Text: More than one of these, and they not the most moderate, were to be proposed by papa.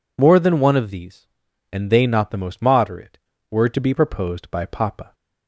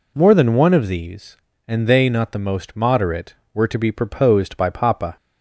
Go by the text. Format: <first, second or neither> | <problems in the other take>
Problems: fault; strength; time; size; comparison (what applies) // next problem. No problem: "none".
neither | none